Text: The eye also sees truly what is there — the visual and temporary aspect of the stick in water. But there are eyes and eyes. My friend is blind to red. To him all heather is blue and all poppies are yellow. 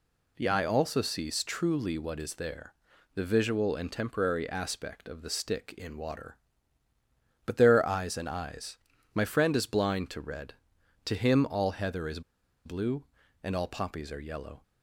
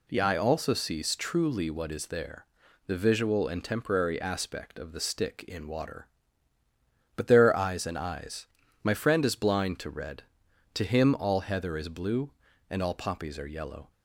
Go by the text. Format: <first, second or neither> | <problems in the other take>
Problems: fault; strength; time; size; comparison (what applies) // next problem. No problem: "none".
second | pauses between "is" and "blue"; at 12.2 s; 0.45 s long